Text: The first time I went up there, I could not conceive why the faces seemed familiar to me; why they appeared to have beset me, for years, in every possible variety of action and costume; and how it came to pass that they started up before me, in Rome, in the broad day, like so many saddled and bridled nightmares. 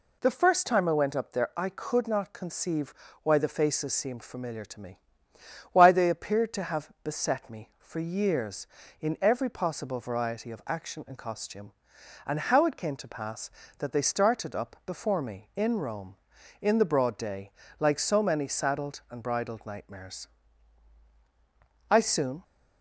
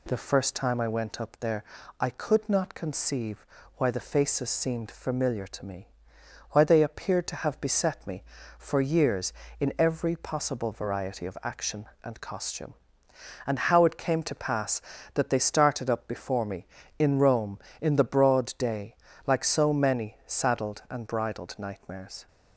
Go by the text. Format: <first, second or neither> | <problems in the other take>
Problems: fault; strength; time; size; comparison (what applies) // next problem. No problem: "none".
second | pauses between "conceive" and "why"; slight; at 2.9 s; 0.30 s long; slight in the second // goes on to say "I soon"; from 21.8 s on; 0.54 s long